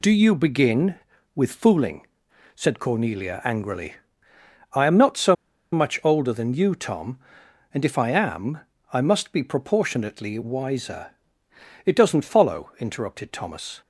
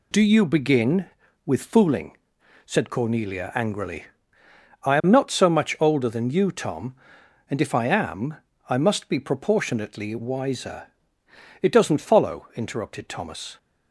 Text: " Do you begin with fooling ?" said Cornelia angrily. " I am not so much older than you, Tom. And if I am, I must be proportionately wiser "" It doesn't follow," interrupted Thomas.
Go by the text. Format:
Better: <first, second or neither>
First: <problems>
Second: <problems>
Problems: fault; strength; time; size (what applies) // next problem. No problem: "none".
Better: second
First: pauses between "so" and "much"; at 5.3 s; 0.37 s long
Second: none